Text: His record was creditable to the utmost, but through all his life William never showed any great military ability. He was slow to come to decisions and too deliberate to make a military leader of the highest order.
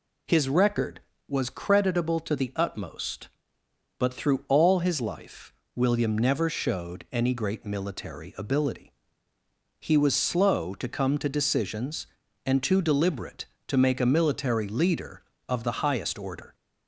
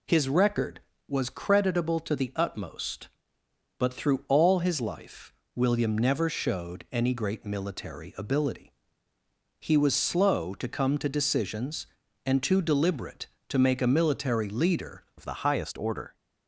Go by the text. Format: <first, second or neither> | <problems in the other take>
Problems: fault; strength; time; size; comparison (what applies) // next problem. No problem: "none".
first | pauses between "life" and "William"; slight; at 5.3 s; 0.22 s long; slight in the first // changes voice at "of"; from 15.1 s on; 1.0 s long